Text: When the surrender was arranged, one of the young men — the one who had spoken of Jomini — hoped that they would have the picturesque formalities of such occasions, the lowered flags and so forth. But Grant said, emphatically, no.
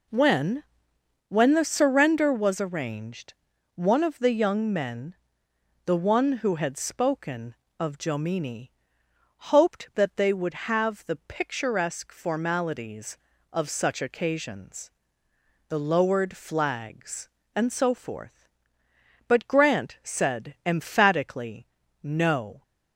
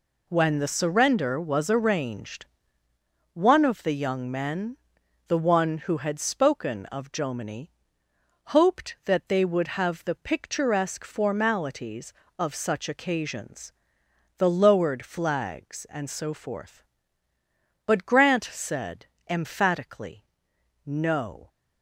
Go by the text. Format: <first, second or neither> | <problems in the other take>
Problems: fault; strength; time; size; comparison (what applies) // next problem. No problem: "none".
second | says "When" twice; at 1.2 s